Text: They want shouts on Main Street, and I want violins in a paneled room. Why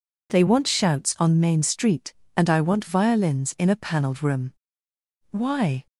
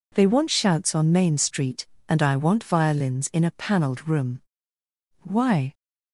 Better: neither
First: none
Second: none

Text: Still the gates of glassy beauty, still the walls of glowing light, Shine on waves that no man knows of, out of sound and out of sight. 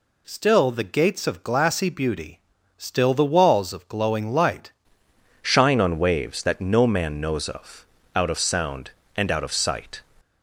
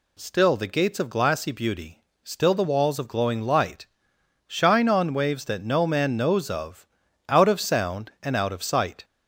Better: second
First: changes voice at "Shine"; from 5.4 s on; 4.6 s long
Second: none

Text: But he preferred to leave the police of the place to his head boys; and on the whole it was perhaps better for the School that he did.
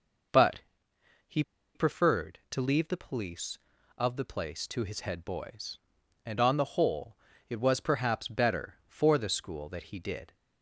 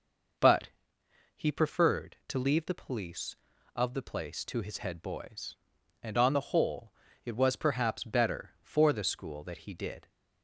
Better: second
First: pauses between "But" and "he"; noticeable; at 0.6 s; 0.66 s long // pauses between "he" and "preferred"; slight; at 1.4 s; 0.33 s long // pauses between "whole" and "it"; slight; at 7.1 s; 0.32 s long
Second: pauses between "But" and "he"; noticeable; at 0.6 s; 0.66 s long // pauses between "whole" and "it"; slight; at 6.9 s; 0.32 s long

